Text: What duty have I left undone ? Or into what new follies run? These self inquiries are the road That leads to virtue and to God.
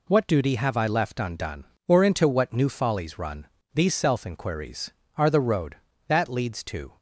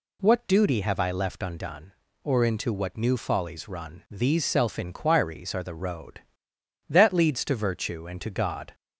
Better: second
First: stops before "virtue and to God"; at 6.9 s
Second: none

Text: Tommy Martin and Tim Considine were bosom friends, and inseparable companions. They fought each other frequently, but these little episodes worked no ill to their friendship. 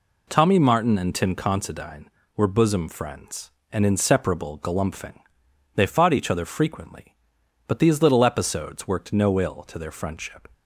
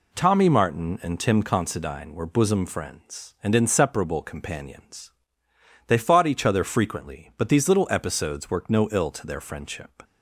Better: second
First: says "galumphing" for "companions"; at 4.5 s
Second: none

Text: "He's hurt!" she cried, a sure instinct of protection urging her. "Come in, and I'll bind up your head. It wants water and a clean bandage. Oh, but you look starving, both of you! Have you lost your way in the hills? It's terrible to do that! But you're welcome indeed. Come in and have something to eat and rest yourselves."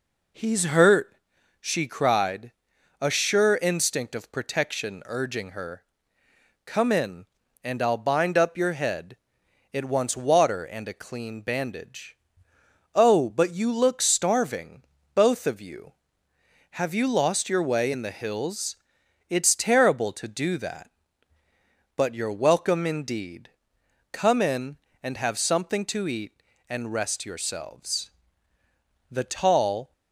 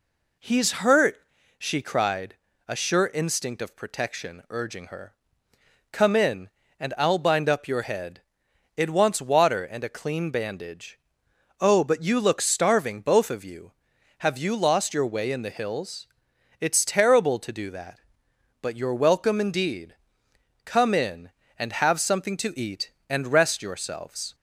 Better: second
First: goes on to say "The tall"; noticeable; from 29.0 s on; 0.82 s long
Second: none

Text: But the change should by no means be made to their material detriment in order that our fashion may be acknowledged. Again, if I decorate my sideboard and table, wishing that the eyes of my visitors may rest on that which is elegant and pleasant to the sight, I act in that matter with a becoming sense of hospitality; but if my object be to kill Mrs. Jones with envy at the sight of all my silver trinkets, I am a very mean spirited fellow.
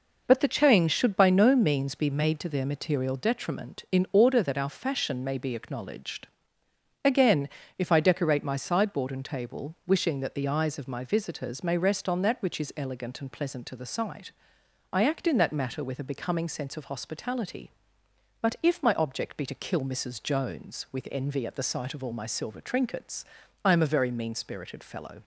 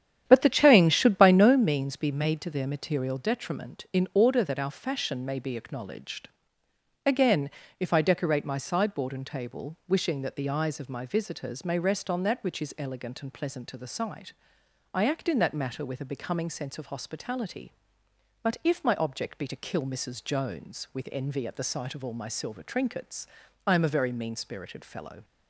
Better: first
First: none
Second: starts louder than the rest; strong; until 1.7 s; 10 dB

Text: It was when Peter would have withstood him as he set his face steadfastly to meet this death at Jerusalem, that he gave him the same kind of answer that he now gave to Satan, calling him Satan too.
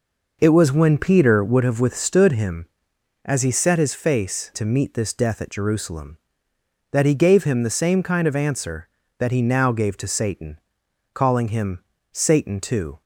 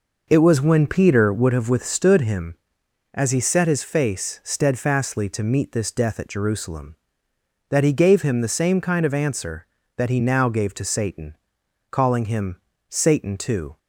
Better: second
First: skips "steadfastly"; at 4.5 s // pauses between "him" and "Satan"; slight; at 11.8 s; 0.30 s long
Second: pauses between "him" and "Satan"; slight; at 12.5 s; 0.30 s long

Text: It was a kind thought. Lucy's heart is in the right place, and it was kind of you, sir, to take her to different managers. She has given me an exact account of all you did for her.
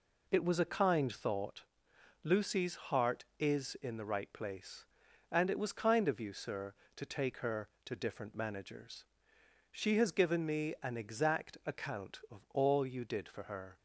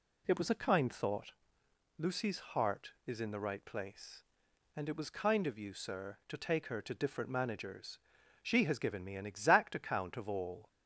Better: first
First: none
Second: stops before "you did for her"; at 10.6 s

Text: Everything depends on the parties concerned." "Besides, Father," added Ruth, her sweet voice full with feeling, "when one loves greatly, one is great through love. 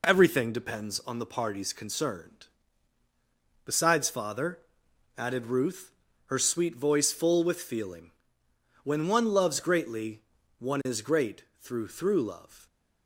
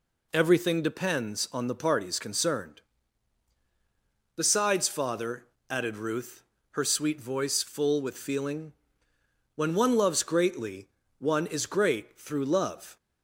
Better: second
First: pauses between "great" and "through"; slight; at 11.4 s; 0.16 s long // says "through" twice; at 11.8 s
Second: none

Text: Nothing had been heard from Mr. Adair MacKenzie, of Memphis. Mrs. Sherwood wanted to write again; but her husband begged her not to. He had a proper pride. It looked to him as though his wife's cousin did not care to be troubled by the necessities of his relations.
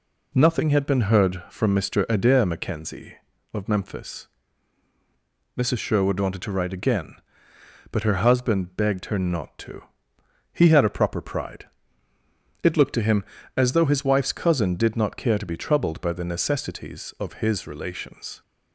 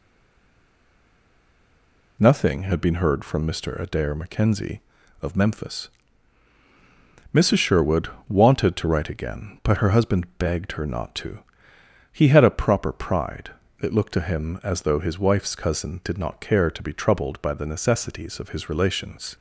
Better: first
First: none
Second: stays silent before the first word; until 2.1 s; 2.1 s long // pauses between "Sherwood" and "wanted"; slight; at 8.0 s; 0.20 s long

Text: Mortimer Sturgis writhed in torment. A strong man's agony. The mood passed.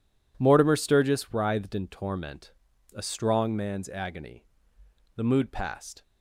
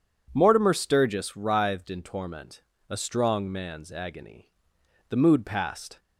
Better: neither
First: none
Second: none

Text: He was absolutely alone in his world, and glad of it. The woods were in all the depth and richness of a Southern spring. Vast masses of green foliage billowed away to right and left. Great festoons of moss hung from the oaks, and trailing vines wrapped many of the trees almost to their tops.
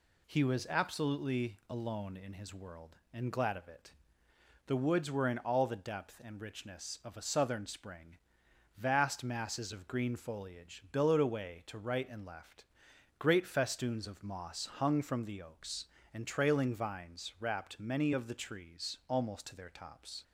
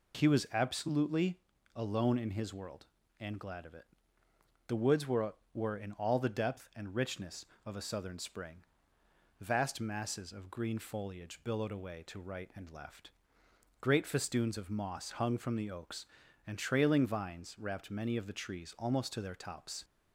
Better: first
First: none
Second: pauses between "absolutely" and "alone"; slight; at 1.3 s; 0.36 s long // says "were" twice; at 5.5 s

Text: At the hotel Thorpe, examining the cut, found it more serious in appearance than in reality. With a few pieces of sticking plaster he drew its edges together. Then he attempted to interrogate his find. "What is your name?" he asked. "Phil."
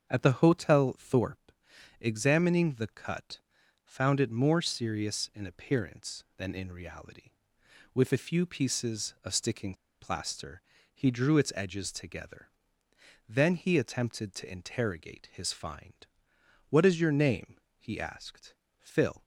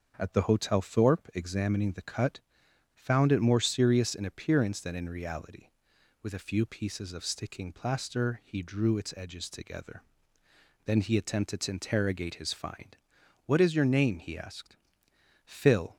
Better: second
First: starts louder than the rest; until 1.1 s; 6.5 dB // pauses between "sticking" and "plaster"; slight; at 9.7 s; 0.26 s long // pauses between "plaster" and "he"; slight; at 10.6 s; 0.32 s long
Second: starts louder than the rest; until 1.1 s; 6.5 dB

